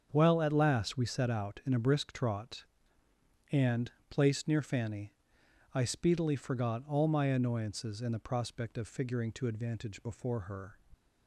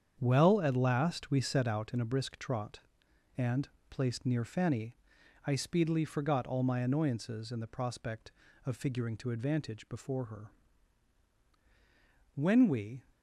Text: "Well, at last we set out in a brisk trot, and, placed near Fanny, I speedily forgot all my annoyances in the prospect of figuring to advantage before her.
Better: first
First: starts louder than the rest; until 1.1 s; 6.5 dB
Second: starts louder than the rest; strong; until 1.2 s; 8 dB // goes on to say "When we"; noticeable; from 12.3 s on; 0.70 s long

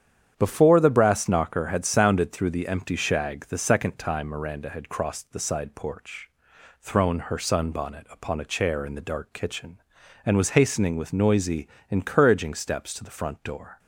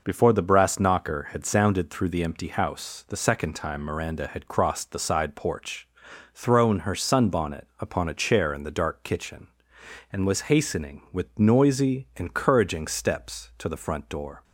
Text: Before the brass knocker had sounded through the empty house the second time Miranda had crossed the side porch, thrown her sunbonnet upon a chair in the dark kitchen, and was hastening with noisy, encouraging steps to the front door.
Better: second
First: starts louder than the rest; strong; until 1.3 s; 9 dB // says "shag" for "house"; at 2.9 s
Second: none

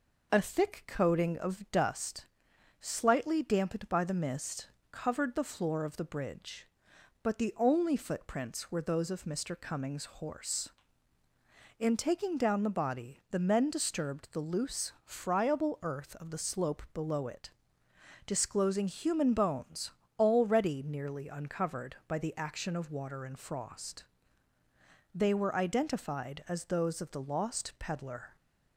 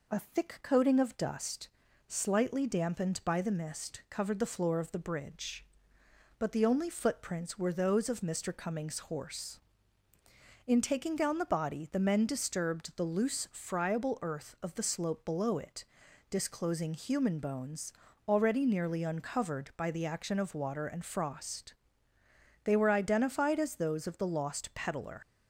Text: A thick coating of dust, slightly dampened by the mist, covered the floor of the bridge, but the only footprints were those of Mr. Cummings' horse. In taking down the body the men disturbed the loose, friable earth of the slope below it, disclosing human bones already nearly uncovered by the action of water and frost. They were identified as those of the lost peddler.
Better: first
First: pauses between "bones" and "already"; slight; at 19.8 s; 0.30 s long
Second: pauses between "bones" and "already"; slight; at 17.9 s; 0.34 s long // leaves "peddler" unfinished; at 25.2 s; 55 ms

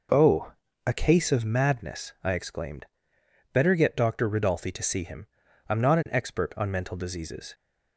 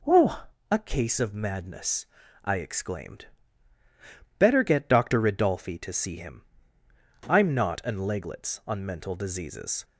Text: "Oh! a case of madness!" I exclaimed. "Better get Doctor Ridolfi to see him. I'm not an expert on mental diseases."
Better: first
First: none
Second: says "leglets" for "expert"; at 7.9 s

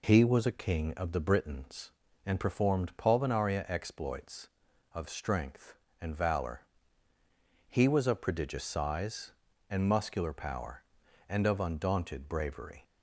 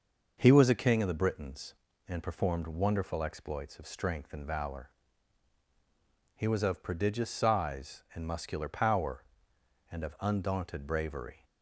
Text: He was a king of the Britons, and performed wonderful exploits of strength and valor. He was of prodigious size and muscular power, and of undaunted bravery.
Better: second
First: says "pulvinaria" for "wonderful"; at 2.9 s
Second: none

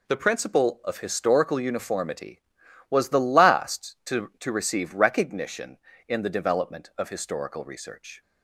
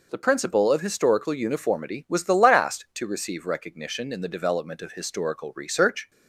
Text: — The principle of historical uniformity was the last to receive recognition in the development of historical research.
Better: second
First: says "to" twice; at 4.3 s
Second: none

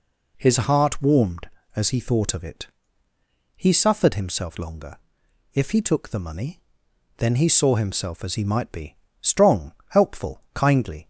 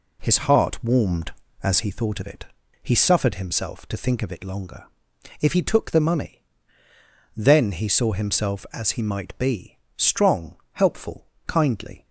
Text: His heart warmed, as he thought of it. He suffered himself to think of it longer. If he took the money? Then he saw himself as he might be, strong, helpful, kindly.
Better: second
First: skips "to think of it"; at 4.5 s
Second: none

